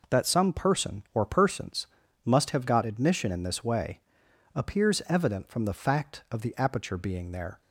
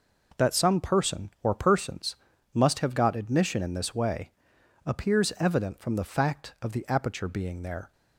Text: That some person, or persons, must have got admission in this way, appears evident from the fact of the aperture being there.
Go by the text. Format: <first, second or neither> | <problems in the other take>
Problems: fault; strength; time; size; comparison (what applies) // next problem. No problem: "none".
neither | none